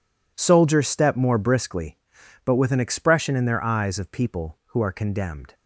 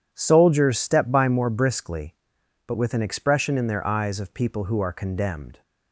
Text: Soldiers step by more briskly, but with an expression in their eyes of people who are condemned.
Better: second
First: skips "by"; at 1.1 s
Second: none

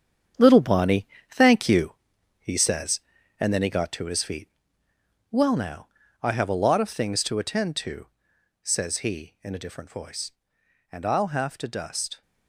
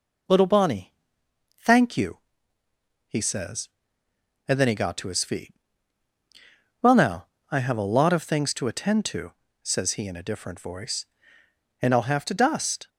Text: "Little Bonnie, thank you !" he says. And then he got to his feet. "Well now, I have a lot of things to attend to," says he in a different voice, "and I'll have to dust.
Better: second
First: gets quieter; noticeable; throughout; 4.5 dB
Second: none

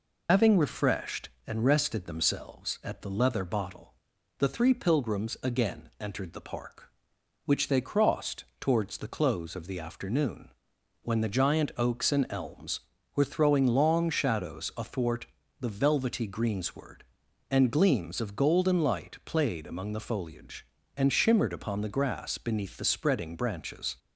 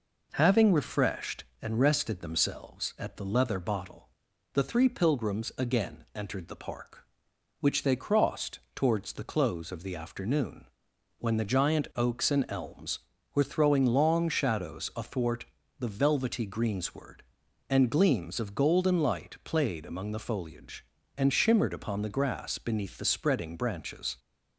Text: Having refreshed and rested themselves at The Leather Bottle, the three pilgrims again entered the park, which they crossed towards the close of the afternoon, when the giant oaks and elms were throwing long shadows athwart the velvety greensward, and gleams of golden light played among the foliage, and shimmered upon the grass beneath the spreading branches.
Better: second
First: loses the start of "Having"; at 0.2 s; 130 ms // pauses between "athwart" and "the"; slight; at 15.2 s; 0.32 s long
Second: pauses between "athwart" and "the"; slight; at 15.4 s; 0.32 s long

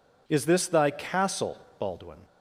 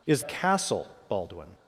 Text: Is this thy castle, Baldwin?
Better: first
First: none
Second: skips "this thy"; at 0.2 s

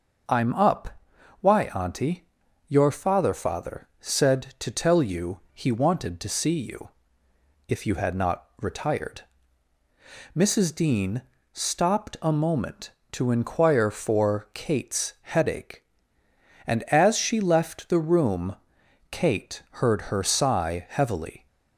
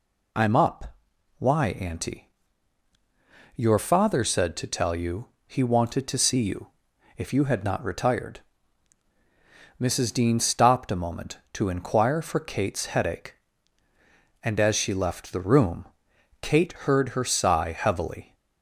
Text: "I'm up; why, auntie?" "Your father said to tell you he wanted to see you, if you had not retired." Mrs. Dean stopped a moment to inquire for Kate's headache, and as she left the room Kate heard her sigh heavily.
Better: second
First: says "father" twice; at 3.3 s // pauses between "you" and "he"; slight; at 5.3 s; 0.16 s long // pauses between "Dean" and "stopped"; slight; at 11.2 s; 0.30 s long // pauses between "room" and "Kate"; noticeable; at 18.5 s; 0.56 s long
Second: pauses between "you" and "he"; slight; at 5.2 s; 0.18 s long // pauses between "room" and "Kate"; noticeable; at 15.8 s; 0.54 s long

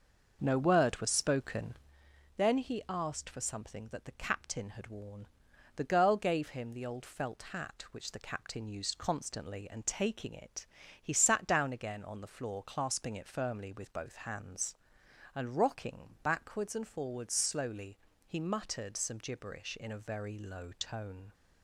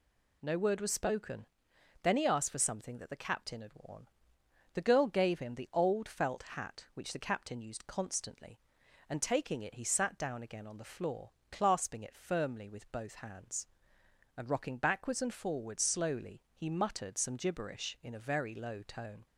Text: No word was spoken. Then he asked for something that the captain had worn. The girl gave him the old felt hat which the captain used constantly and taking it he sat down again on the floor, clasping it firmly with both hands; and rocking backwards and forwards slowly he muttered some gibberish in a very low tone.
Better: second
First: starts louder than the rest; noticeable; until 1.9 s; 6 dB // pauses between "it" and "he"; at 10.6 s; 0.38 s long // pauses between "slowly" and "he"; slight; at 17.9 s; 0.30 s long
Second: none

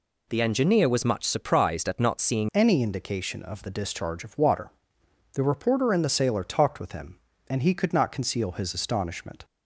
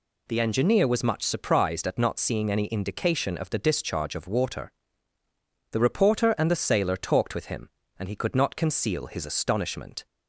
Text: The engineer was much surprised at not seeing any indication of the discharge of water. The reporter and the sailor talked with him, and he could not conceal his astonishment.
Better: second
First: changes voice at "any"; from 2.5 s on; 6.9 s long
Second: none

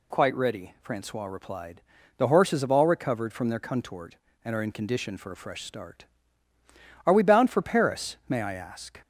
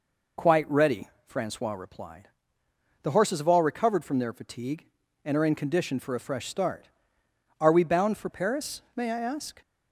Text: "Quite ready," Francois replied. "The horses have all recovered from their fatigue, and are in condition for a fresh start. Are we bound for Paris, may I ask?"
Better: second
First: says "contort" for "fatigue"; at 3.5 s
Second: none

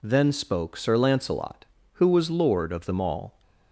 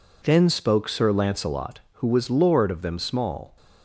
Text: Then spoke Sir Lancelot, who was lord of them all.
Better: first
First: none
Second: says "small" for "all"; at 2.9 s

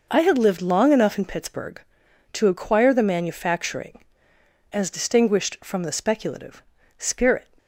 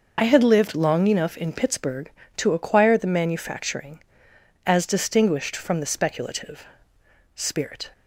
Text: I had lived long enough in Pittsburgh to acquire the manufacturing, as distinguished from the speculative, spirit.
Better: first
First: none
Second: loses the start of "I"; at 0.1 s; 40 ms

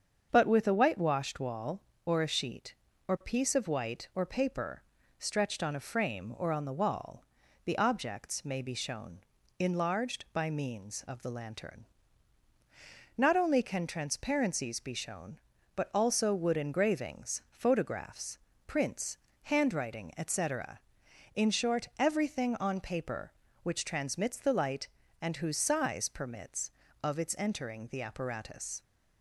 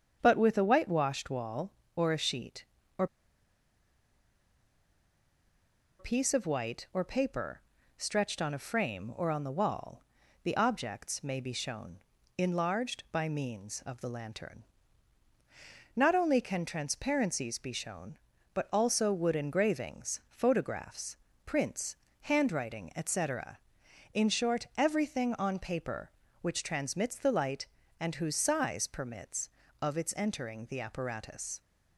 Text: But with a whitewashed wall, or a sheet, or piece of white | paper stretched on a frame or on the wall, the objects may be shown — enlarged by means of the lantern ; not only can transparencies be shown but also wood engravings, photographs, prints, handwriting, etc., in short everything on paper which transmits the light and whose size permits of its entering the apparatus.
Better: first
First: starts louder than the rest; until 1.3 s; 7 dB // pauses between "paper" and "stretched"; slight; at 4.8 s; 0.36 s long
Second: starts louder than the rest; until 1.2 s; 7 dB // pauses between "or" and "piece"; strong; at 3.0 s; 2.9 s long // pauses between "paper" and "stretched"; slight; at 7.6 s; 0.36 s long

